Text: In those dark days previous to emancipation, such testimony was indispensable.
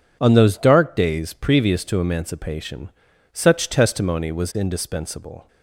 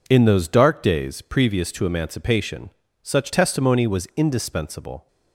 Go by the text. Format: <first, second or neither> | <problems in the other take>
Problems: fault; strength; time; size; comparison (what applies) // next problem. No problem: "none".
second | says "On" for "In"; at 0.2 s